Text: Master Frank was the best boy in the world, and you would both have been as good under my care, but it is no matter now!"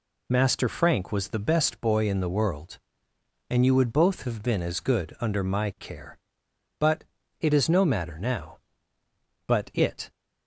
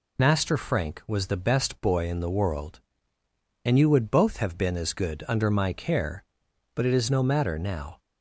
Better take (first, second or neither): second